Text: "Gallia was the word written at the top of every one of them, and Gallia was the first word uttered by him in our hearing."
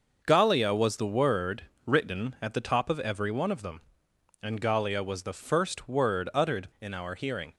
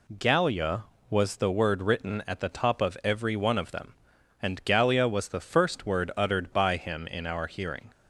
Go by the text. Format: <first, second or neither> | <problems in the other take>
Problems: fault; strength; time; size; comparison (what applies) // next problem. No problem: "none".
second | starts louder than the rest; until 1.2 s; 6 dB // pauses between "word" and "written"; slight; at 1.6 s; 0.20 s long // skips "by him"; at 6.7 s